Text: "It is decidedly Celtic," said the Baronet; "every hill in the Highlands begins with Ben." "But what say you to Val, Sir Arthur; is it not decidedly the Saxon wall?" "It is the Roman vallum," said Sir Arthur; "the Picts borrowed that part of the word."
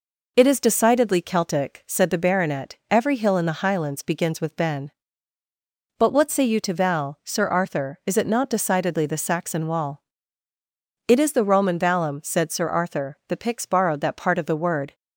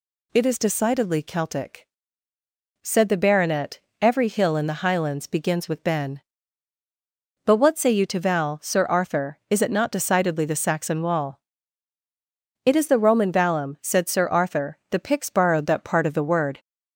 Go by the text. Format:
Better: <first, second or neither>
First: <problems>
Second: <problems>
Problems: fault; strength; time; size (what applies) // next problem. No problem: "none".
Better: neither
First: none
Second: none